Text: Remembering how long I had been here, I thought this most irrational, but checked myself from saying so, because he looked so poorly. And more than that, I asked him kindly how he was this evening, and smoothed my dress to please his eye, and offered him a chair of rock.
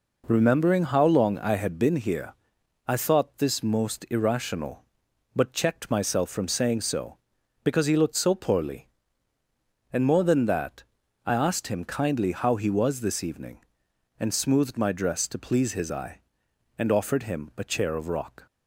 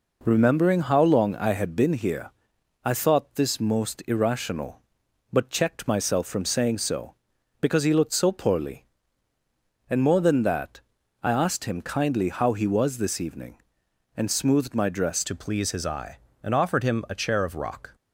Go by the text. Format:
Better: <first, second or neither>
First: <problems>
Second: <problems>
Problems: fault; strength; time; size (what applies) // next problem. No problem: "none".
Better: first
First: none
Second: changes voice at "to"; from 15.2 s on; 2.7 s long